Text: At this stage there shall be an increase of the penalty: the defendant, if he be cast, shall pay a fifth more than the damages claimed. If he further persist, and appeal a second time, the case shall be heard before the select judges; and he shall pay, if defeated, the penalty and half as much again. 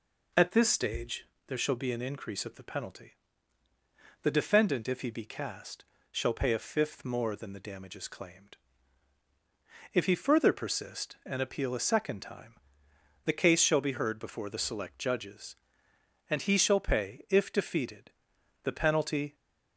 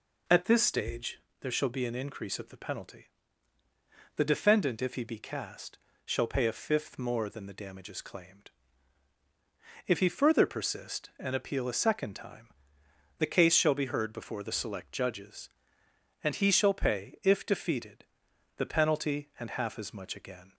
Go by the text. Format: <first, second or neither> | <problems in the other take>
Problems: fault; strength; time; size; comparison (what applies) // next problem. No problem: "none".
second | pauses between "stage" and "there"; slight; at 1.2 s; 0.20 s long; slight in the second // stops before "and half as much again"; at 19.3 s